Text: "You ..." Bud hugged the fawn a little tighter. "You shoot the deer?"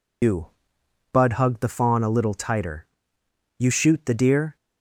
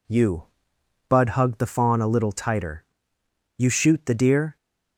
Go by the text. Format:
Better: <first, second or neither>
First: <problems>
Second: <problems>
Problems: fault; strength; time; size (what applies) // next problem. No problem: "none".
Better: second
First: loses the start of "You"; at 0.2 s; 115 ms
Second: none